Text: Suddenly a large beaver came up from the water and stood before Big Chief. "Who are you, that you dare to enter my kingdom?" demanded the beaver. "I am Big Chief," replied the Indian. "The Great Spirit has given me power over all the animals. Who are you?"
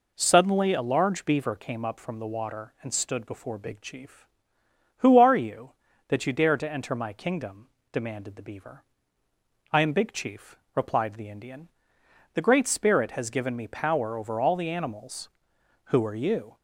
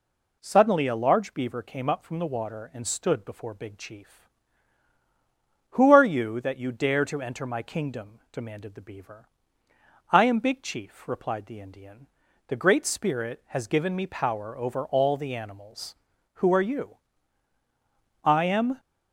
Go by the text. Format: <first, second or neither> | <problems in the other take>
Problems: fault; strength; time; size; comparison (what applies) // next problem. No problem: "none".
first | goes on to say "I am"; from 18.2 s on; 0.56 s long